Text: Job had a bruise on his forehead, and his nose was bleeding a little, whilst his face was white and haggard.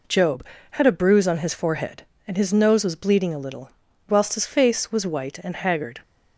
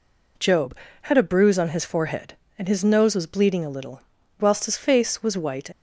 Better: first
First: none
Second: stops before "and haggard"; at 5.7 s

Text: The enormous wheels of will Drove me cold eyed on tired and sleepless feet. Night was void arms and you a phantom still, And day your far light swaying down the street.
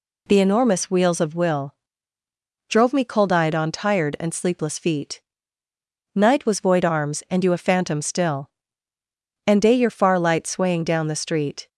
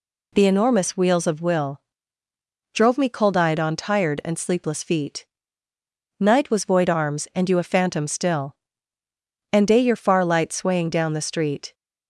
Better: neither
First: pauses between "will" and "Drove"; noticeable; at 1.7 s; 0.96 s long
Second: pauses between "will" and "Drove"; noticeable; at 1.7 s; 0.94 s long

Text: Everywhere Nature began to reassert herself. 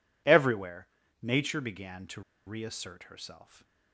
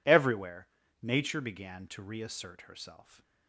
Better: second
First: pauses between "Everywhere" and "Nature"; slight; at 0.8 s; 0.36 s long // pauses between "to" and "reassert"; slight; at 2.2 s; 0.26 s long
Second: pauses between "Everywhere" and "Nature"; slight; at 0.6 s; 0.36 s long

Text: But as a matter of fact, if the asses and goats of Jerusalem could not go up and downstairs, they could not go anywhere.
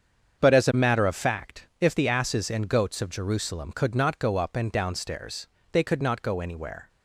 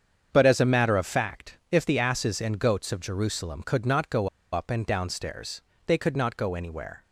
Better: first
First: starts louder than the rest; strong; until 1.4 s; 7.5 dB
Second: starts louder than the rest; strong; until 1.3 s; 7.5 dB // pauses between "go" and "up"; slight; at 4.2 s; 0.23 s long

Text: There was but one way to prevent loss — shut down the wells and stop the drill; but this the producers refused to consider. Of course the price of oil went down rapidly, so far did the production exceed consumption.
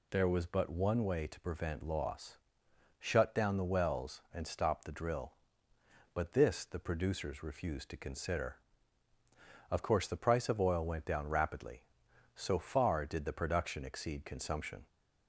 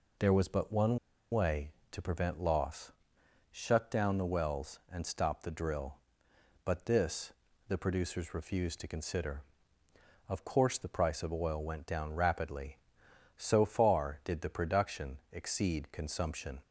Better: first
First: none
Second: pauses between "one" and "way"; slight; at 0.9 s; 0.34 s long // pauses between "this" and "the"; at 7.3 s; 0.38 s long

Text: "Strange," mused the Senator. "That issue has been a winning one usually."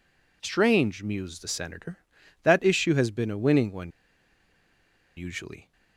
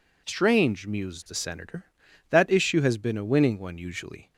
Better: second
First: pauses between "one" and "usually"; strong; at 3.8 s; 1.2 s long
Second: none

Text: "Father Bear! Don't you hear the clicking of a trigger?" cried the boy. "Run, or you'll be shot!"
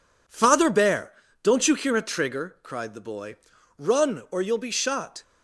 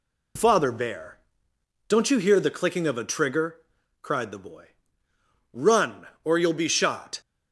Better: second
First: skips "the clicking of"; at 1.9 s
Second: none

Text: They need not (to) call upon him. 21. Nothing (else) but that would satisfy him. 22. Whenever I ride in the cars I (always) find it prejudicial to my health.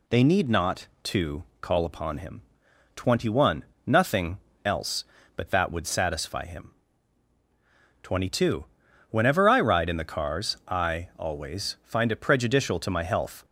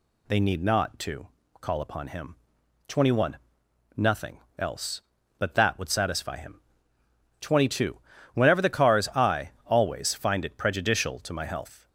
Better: first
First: none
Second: skips "I ride in"; at 8.6 s

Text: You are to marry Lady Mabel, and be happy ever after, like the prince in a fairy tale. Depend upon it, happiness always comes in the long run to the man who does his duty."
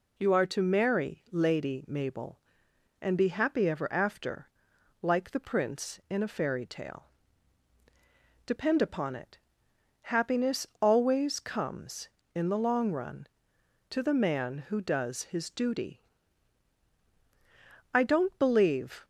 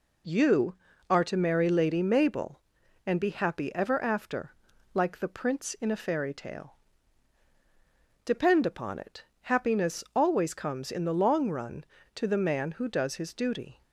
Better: second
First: goes on to say "I don't believe"; noticeable; from 17.9 s on; 1.1 s long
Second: none

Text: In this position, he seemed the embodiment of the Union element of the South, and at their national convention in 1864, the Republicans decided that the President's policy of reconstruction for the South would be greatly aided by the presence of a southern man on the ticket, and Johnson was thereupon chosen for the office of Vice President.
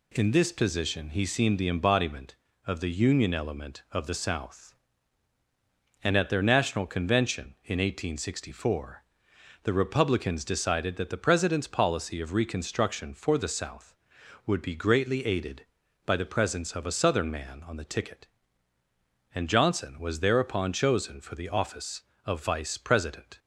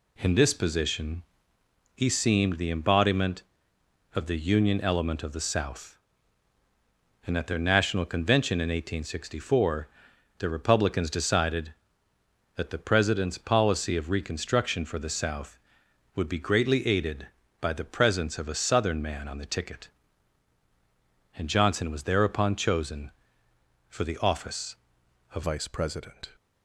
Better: first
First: none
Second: changes voice at "Vice"; from 25.4 s on; 0.9 s long

